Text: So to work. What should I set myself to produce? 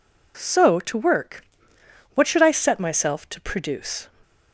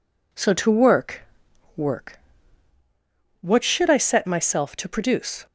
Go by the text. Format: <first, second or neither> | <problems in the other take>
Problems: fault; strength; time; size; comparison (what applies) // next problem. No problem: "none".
first | says "work" twice; at 1.7 s